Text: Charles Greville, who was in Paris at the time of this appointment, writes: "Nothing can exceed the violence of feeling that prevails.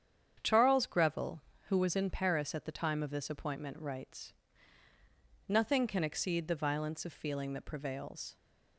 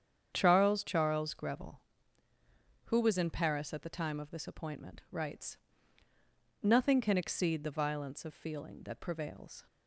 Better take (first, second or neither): first